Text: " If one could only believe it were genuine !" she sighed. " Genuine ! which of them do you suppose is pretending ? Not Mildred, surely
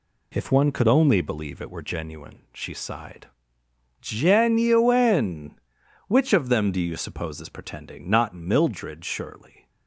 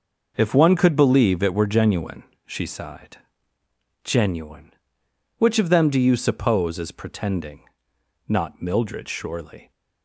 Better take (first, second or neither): first